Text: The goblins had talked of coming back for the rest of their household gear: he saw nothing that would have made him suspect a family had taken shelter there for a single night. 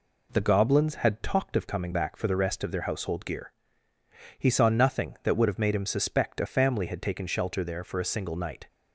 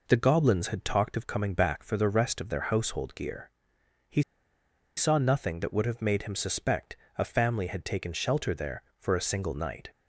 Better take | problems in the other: first | pauses between "he" and "saw"; noticeable; at 4.2 s; 0.75 s long // pauses between "suspect" and "a"; slight; at 6.9 s; 0.22 s long

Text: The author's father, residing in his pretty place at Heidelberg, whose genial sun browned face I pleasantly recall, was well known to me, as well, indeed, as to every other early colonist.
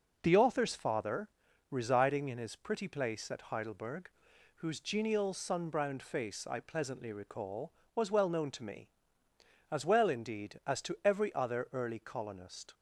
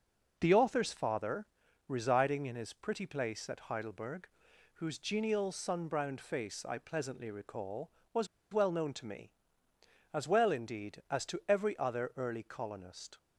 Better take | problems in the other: first | pauses between "was" and "well"; slight; at 8.2 s; 0.25 s long

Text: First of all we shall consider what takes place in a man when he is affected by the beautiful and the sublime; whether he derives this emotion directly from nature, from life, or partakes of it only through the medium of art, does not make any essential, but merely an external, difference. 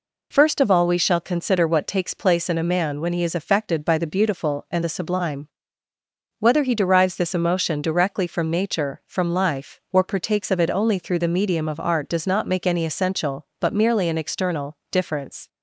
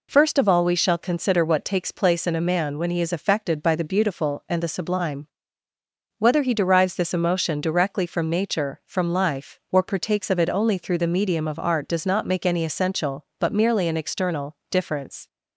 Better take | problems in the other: neither | none

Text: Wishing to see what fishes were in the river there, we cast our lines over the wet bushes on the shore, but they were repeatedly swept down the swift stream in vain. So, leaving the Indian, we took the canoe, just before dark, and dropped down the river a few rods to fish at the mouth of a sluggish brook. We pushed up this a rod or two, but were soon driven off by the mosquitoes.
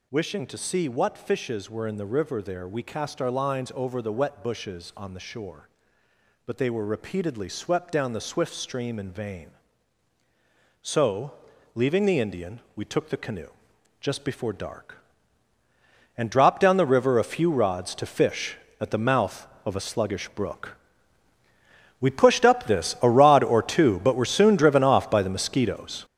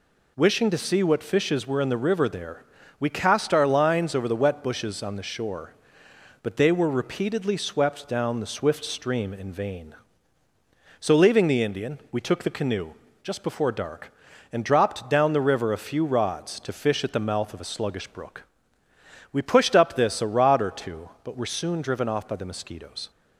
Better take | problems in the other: second | gets louder; strong; throughout; 9 dB

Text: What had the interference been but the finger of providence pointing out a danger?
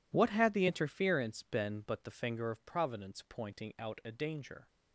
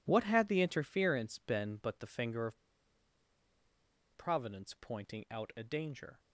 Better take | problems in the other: first | pauses between "of" and "providence"; strong; at 2.5 s; 1.5 s long

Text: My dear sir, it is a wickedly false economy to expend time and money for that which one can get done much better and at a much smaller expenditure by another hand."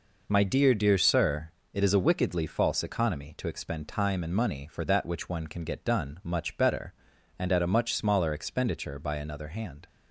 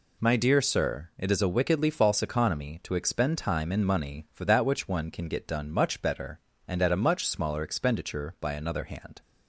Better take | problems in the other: second | says "dear" twice; at 0.7 s

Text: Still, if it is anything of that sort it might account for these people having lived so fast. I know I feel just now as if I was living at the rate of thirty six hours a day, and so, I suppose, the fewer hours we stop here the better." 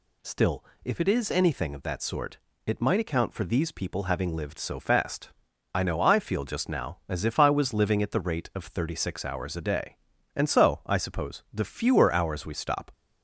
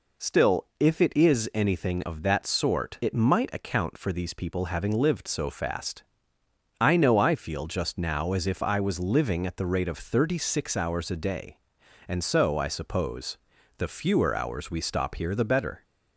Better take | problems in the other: second | pauses between "sort" and "it"; slight; at 2.3 s; 0.28 s long // stops before "here the better"; at 12.9 s

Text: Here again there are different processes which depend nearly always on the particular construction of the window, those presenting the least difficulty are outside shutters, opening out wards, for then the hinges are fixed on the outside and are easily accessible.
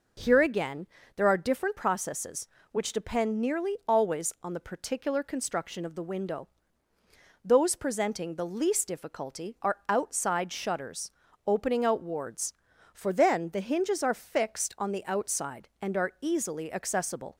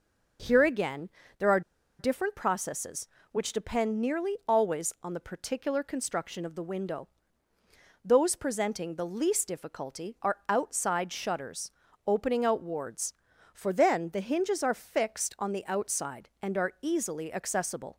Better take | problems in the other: first | pauses between "again" and "there"; slight; at 1.1 s; 0.26 s long; slight in the first // pauses between "are" and "different"; at 1.6 s; 0.38 s long

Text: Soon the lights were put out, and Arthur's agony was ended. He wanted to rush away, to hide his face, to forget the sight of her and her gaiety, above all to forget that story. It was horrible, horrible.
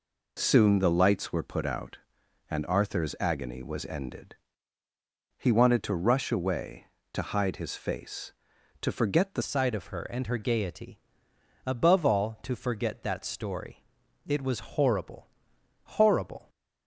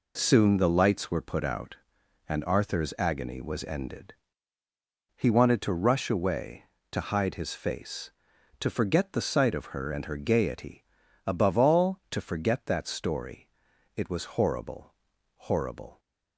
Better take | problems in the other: second | changes voice at "sight"; from 9.4 s on; 7.0 s long

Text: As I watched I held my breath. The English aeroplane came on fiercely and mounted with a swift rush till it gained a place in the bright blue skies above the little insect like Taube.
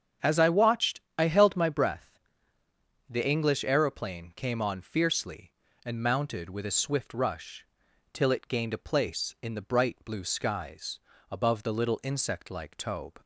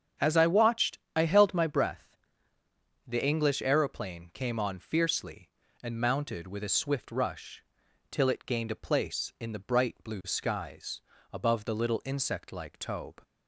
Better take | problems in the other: neither | starts louder than the rest; strong; the same in both // pauses between "watched" and "I"; slight; the same in both // pauses between "rush" and "till"; noticeable; the same in both // pauses between "skies" and "above"; slight; the same in both

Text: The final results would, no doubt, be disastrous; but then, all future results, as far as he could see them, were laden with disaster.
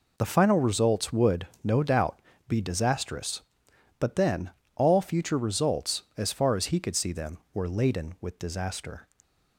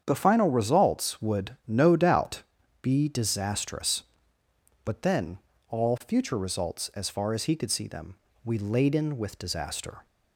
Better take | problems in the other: first | starts louder than the rest; strong; until 1.0 s; 8 dB // says "we" for "were"; at 8.4 s

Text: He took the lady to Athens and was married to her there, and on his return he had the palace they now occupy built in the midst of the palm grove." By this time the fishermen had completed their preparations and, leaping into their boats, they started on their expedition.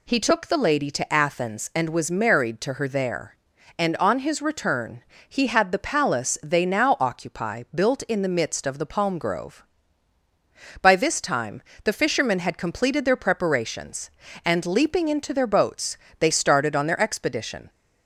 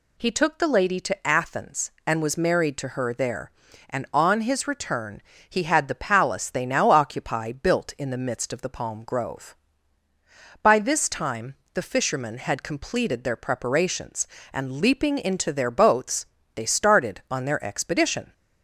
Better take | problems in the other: neither | pauses between "return" and "he"; slight; the same in both // pauses between "time" and "the"; slight; the same in both

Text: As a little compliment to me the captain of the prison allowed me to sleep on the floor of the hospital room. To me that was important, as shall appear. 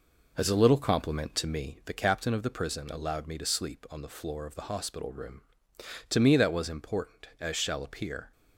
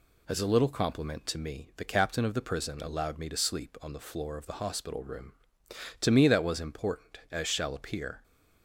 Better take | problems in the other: second | starts louder than the rest; noticeable; until 1.9 s; 4.5 dB

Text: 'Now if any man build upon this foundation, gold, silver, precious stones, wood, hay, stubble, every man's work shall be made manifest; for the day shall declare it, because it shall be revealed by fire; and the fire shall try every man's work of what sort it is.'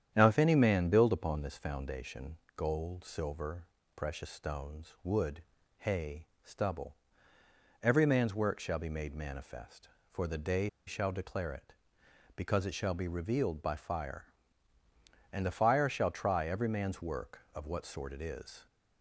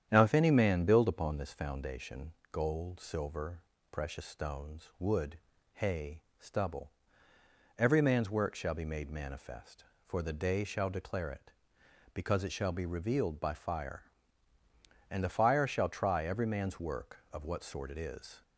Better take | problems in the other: second | starts louder than the rest; strong; until 1.1 s; 9.5 dB; strong in the second // pauses between "day" and "shall"; slight; at 10.6 s; 0.19 s long

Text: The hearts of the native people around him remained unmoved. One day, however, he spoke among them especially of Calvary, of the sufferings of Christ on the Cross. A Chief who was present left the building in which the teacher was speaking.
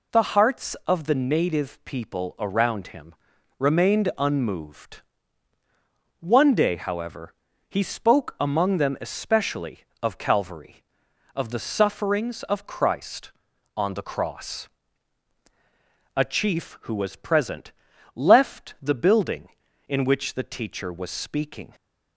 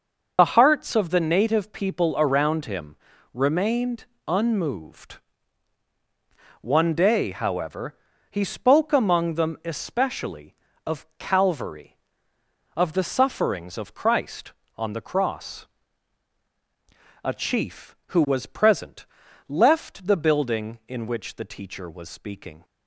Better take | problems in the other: first | loses the start of "The"; at 0.3 s; 45 ms // pauses between "him" and "remained"; at 2.9 s; 0.38 s long; noticeable in the first // pauses between "remained" and "unmoved"; slight; at 4.0 s; 0.22 s long // pauses between "present" and "left"; at 19.0 s; 0.40 s long; also in the first

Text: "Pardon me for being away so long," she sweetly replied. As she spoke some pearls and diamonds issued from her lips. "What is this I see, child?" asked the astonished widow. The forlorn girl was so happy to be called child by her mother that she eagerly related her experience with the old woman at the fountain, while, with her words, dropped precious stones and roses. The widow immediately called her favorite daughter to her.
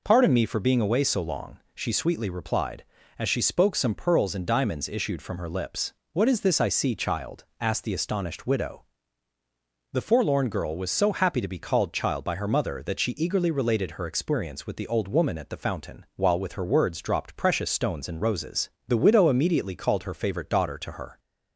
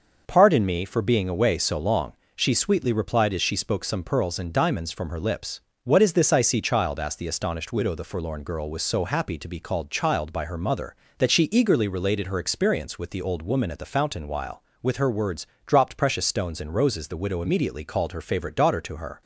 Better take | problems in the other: first | skips "issued"; at 4.8 s

